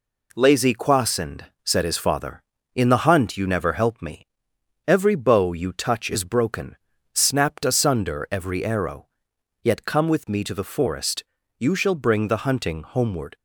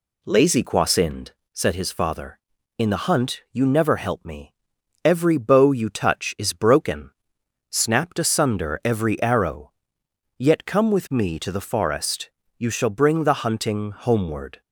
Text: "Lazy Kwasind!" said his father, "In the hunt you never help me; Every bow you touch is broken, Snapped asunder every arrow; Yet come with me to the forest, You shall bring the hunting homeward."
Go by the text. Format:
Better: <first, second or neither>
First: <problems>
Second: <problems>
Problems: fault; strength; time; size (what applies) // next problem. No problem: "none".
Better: neither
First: none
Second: none